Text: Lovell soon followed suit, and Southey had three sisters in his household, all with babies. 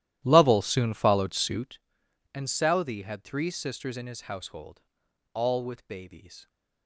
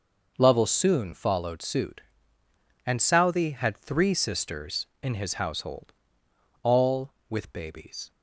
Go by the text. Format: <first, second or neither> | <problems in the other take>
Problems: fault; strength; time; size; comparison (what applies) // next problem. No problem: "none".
second | starts louder than the rest; strong; until 1.8 s; 13 dB